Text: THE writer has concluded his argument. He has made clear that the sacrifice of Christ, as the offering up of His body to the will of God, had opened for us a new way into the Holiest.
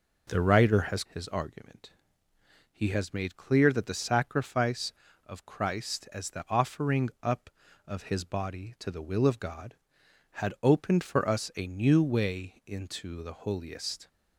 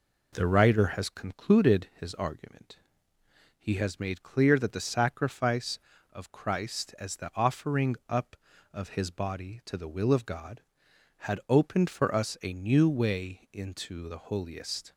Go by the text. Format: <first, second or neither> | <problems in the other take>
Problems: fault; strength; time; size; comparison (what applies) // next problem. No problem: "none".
second | skips "concluded"; at 1.0 s